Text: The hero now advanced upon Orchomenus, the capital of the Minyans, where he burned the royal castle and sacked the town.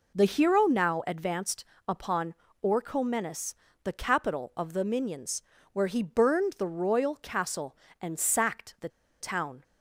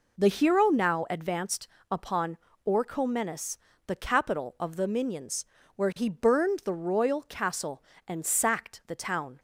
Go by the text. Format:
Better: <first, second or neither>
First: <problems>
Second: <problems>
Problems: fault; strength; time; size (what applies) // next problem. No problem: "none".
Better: second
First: pauses between "advanced" and "upon"; slight; at 1.6 s; 0.24 s long // pauses between "upon" and "Orchomenus"; slight; at 2.3 s; 0.28 s long // pauses between "the" and "town"; slight; at 8.8 s; 0.31 s long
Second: pauses between "advanced" and "upon"; slight; at 1.6 s; 0.24 s long // pauses between "upon" and "Orchomenus"; slight; at 2.3 s; 0.28 s long